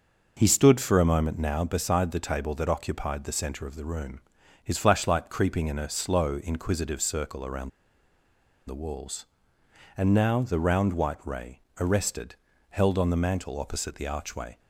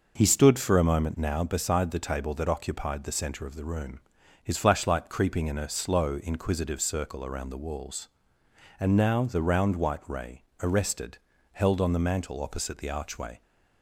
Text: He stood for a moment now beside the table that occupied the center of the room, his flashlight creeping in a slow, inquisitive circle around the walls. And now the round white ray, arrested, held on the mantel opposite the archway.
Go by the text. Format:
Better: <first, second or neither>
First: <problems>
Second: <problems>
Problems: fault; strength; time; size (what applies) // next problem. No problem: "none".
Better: second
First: pauses between "around" and "the"; noticeable; at 7.6 s; 0.97 s long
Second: none